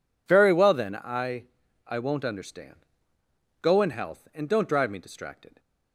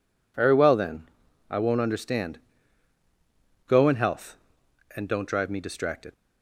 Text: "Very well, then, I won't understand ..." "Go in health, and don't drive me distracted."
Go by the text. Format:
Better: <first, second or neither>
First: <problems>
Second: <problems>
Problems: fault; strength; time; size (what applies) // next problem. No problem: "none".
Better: second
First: says "I" twice; at 1.8 s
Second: none